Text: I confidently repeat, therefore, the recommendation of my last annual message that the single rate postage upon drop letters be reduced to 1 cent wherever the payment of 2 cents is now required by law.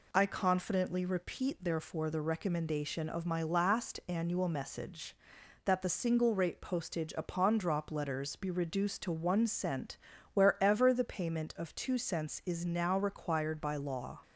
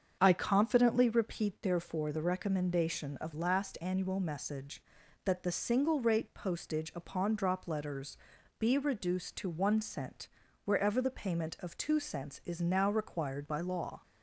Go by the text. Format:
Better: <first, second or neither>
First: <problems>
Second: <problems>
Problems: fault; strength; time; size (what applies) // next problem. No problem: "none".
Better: first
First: pauses between "cent" and "wherever"; slight; at 9.9 s; 0.36 s long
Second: starts louder than the rest; strong; until 1.2 s; 7 dB // skips "my"; at 3.3 s // pauses between "letters" and "be"; at 8.1 s; 0.44 s long // pauses between "cent" and "wherever"; slight; at 10.2 s; 0.36 s long